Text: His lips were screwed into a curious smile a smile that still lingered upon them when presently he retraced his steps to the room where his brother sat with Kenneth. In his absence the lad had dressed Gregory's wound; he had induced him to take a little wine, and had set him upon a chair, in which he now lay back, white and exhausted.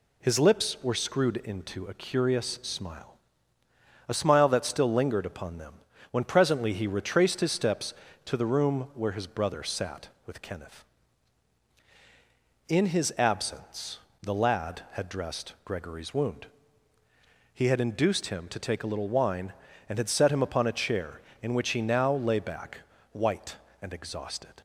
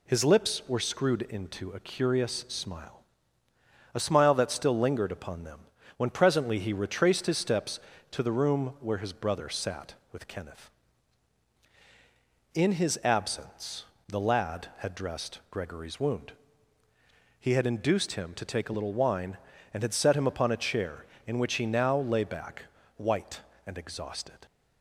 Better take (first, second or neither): neither